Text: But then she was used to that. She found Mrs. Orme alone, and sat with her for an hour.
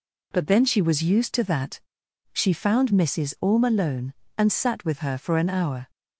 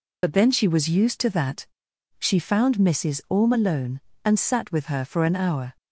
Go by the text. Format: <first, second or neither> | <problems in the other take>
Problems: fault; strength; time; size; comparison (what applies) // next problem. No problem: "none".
first | loses the start of "But"; at 0.2 s; 50 ms